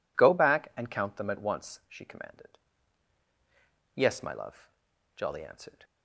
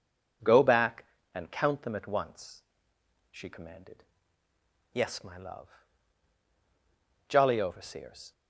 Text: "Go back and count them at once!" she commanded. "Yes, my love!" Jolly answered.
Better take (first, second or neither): first